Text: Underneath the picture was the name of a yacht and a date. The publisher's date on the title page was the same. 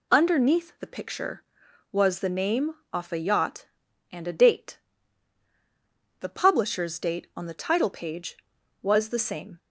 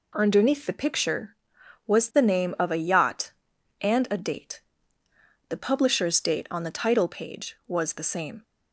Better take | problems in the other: second | says "off" for "of"; at 2.9 s

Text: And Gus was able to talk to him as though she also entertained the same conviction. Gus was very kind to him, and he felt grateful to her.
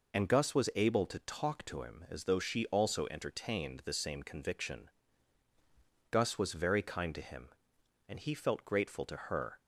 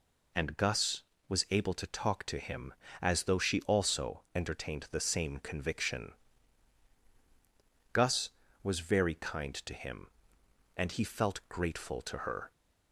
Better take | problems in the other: neither | none

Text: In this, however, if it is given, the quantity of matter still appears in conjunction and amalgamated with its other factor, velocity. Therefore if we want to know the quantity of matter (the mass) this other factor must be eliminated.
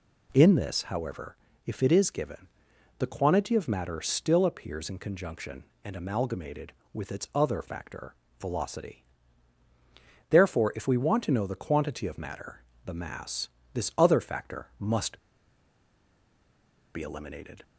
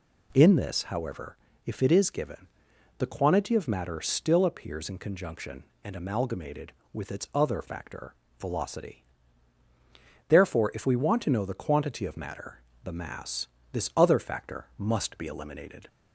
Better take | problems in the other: second | pauses between "must" and "be"; strong; at 15.1 s; 1.7 s long

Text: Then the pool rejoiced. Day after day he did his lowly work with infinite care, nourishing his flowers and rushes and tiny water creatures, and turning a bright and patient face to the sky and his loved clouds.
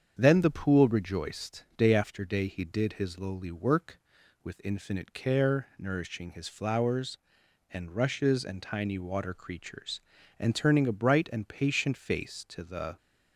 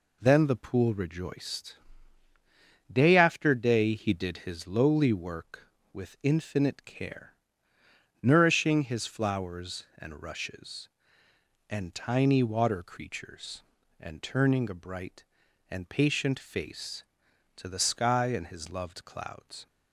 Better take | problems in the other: second | starts louder than the rest; strong; until 1.1 s; 7.5 dB // stops before "sky and his loved clouds"; at 12.9 s

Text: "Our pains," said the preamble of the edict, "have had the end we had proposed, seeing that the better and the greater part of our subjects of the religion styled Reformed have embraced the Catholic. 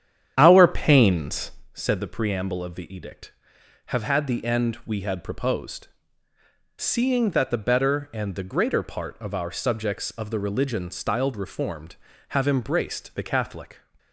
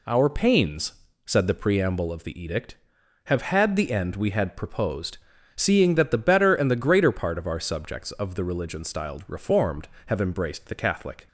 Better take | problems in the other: second | starts louder than the rest; strong; until 1.7 s; 9.5 dB

